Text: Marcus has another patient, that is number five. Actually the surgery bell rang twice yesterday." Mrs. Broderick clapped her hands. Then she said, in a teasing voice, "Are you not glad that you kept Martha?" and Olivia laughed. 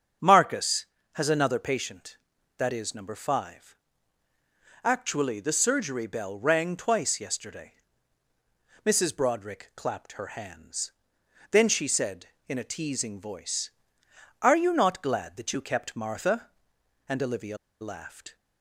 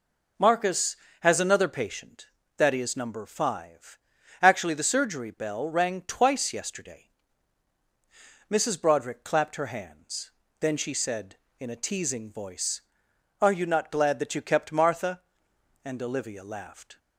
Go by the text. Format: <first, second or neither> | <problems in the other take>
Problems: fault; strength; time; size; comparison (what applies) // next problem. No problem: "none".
second | starts louder than the rest; strong; until 1.5 s; 7.5 dB // pauses between "Olivia" and "laughed"; slight; at 17.5 s; 0.24 s long